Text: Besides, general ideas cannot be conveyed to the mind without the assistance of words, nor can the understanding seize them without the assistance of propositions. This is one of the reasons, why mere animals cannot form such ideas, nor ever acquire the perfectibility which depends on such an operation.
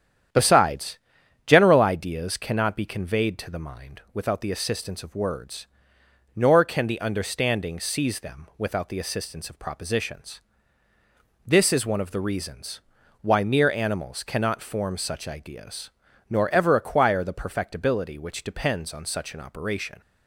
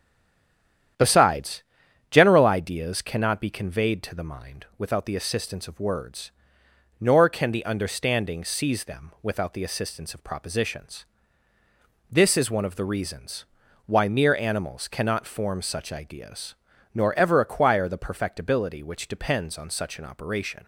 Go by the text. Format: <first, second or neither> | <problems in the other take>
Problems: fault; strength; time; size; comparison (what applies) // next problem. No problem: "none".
first | stays silent before the first word; until 0.9 s; 0.9 s long // starts louder than the rest; strong; until 2.4 s; 10 dB; strong in the first